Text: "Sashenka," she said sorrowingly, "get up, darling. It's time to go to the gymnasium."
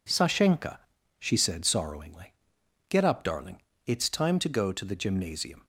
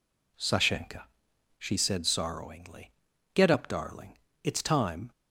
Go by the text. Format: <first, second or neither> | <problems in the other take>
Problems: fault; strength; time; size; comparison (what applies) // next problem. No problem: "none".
first | stops before "to go to the gymnasium"; at 5.1 s